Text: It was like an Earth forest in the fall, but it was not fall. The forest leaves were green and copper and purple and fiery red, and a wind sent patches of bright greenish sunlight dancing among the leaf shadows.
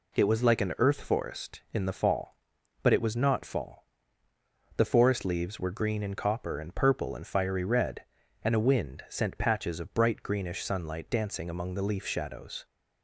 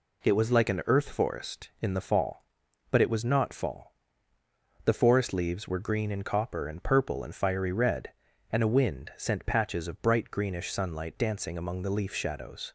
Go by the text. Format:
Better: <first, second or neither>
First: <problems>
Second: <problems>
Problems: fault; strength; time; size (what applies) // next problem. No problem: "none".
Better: neither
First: none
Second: none